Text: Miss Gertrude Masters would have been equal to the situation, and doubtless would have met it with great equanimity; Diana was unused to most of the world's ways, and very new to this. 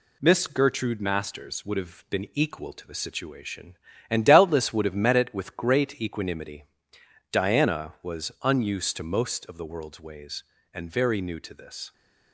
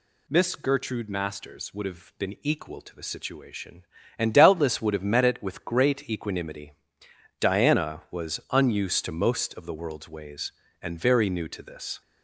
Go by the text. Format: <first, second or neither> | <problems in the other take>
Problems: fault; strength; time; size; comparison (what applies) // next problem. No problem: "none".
second | gets quieter; slight; throughout; 3 dB